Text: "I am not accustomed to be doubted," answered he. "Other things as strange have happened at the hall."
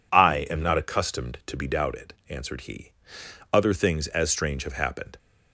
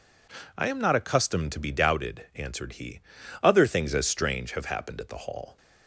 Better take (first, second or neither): second